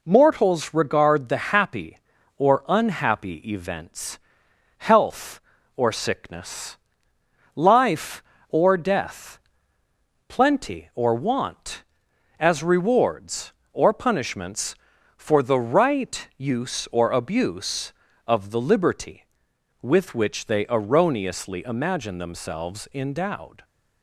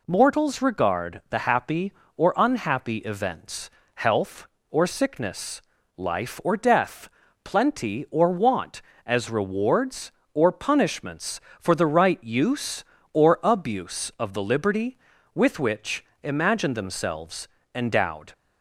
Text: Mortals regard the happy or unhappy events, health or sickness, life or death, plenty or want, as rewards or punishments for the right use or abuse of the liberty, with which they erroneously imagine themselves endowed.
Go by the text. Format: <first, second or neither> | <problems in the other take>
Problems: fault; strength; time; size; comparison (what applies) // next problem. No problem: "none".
first | skips "they erroneously"; at 16.1 s // pauses between "themselves" and "endowed"; slight; at 17.4 s; 0.26 s long